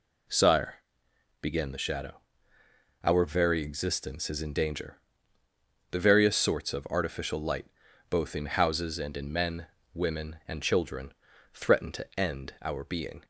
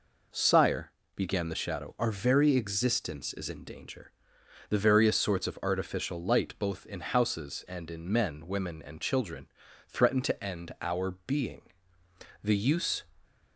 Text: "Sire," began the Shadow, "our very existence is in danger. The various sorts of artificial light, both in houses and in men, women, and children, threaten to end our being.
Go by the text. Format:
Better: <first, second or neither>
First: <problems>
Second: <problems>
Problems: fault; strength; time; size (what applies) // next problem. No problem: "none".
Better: first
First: none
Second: goes on to say "The use"; noticeable; from 12.4 s on; 0.62 s long